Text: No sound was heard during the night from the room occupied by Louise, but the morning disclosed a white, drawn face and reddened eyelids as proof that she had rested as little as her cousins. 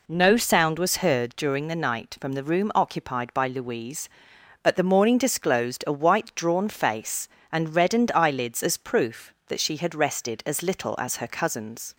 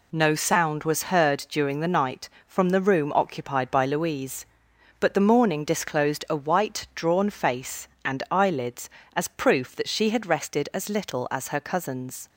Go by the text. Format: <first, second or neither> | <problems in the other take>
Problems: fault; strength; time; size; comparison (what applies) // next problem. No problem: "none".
first | skips "reddened"; at 8.2 s